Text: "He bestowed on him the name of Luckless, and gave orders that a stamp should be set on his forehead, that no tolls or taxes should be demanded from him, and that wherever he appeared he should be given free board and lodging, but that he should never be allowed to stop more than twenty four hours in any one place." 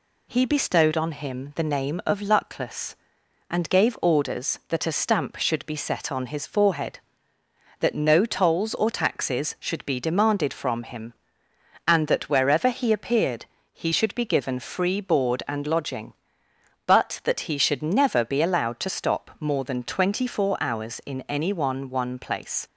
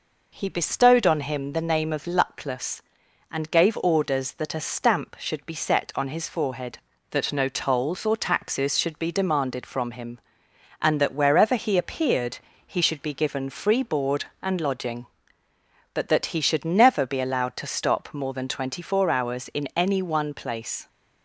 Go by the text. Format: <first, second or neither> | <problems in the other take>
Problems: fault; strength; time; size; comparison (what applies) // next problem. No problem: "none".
second | pauses between "appeared" and "he"; slight; at 13.4 s; 0.26 s long; slight in the second // says "one" twice; at 21.8 s